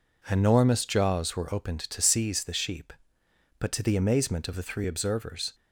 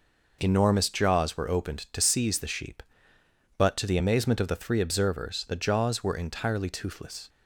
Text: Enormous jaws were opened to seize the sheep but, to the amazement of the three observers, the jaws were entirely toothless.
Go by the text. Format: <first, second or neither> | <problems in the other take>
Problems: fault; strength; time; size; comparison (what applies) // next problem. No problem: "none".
second | stops before "the jaws were entirely toothless"; at 5.5 s